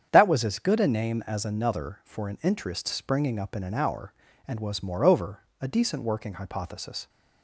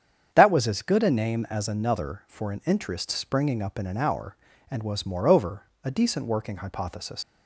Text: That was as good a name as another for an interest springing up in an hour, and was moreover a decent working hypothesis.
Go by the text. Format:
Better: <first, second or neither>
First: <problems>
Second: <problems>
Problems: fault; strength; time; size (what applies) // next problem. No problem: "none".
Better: first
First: starts louder than the rest; strong; until 1.1 s; 8.5 dB // pauses between "moreover" and "a"; slight; at 5.4 s; 0.20 s long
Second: starts louder than the rest; strong; until 1.3 s; 8 dB // pauses between "moreover" and "a"; slight; at 5.6 s; 0.20 s long // leaves "hypothesis" unfinished; at 7.2 s; 90 ms